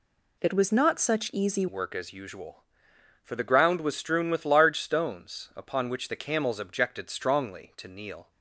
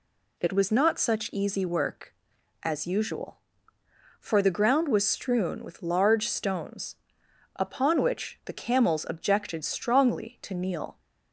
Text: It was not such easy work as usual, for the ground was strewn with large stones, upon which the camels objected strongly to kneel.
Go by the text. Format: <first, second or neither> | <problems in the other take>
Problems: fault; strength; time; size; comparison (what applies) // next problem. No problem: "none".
second | changes voice at "work"; from 1.6 s on; 6.7 s long